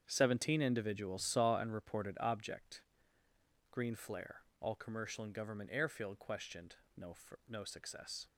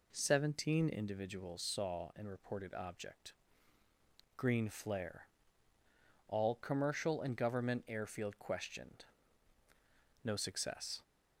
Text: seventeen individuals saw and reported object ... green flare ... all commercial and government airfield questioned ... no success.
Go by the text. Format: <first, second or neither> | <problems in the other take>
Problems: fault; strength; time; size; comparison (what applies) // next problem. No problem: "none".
second | starts louder than the rest; strong; until 1.0 s; 7.5 dB // says "no" twice; at 7.4 s